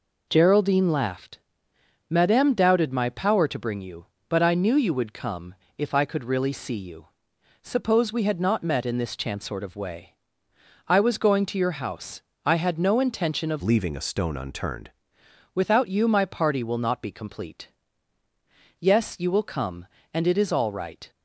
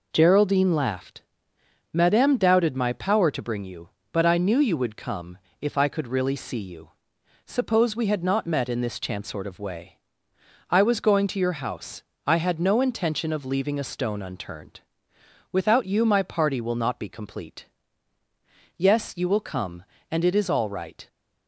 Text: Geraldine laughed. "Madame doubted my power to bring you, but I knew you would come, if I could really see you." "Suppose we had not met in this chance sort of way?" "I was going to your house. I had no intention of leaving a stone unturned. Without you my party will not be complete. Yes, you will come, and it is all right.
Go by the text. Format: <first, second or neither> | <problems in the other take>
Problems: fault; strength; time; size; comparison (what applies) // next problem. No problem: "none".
second | changes voice from "leaving" to "unturned"; from 13.6 to 14.9 s; 1.3 s long